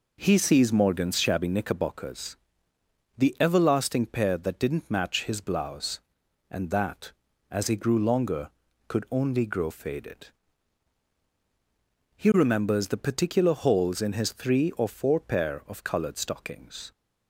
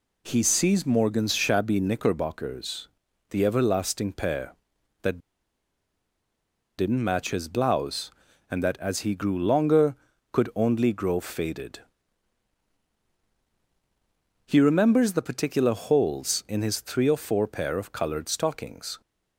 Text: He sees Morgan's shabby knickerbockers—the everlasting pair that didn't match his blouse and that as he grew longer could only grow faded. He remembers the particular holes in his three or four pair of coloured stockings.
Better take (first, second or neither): first